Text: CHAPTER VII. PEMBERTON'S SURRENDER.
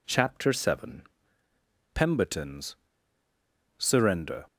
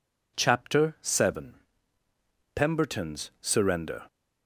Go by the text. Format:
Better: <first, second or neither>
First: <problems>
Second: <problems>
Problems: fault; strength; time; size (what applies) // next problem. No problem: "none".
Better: second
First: pauses between "PEMBERTON'S" and "SURRENDER"; at 2.7 s; 1.0 s long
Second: none